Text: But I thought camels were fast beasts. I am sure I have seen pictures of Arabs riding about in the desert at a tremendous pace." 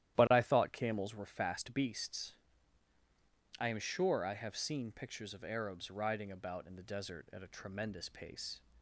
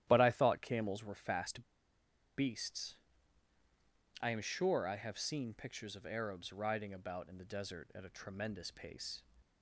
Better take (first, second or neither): first